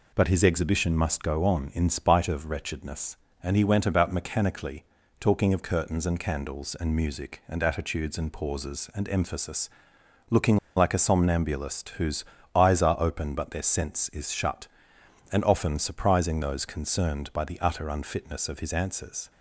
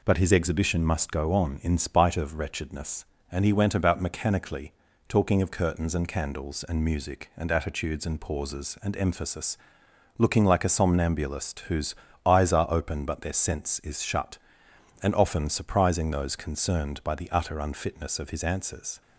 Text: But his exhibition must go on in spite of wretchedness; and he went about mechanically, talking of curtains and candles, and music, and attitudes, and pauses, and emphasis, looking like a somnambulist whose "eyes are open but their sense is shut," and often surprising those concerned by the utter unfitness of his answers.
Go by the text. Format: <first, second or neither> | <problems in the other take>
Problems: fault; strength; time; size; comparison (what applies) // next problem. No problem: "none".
second | pauses between "looking" and "like"; slight; at 10.5 s; 0.19 s long // pauses between "whose" and "eyes"; slight; at 12.2 s; 0.30 s long; slight in the second